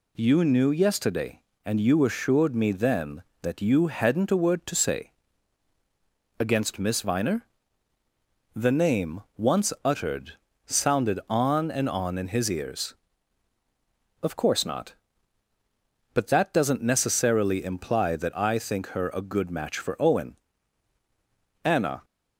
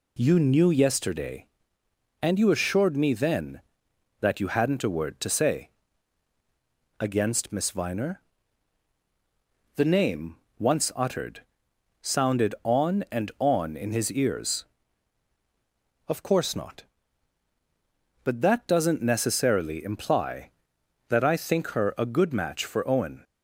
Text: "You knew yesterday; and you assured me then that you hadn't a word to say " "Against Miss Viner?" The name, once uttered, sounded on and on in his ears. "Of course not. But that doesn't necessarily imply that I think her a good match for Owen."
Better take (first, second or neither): second